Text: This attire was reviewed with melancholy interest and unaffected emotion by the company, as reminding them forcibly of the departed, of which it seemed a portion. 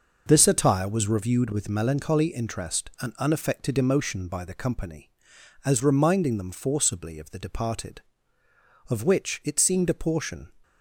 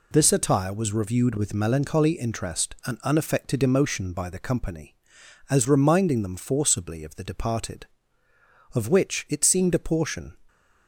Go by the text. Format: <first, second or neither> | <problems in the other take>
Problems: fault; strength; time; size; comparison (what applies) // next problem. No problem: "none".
second | starts louder than the rest; noticeable; until 1.4 s; 5.5 dB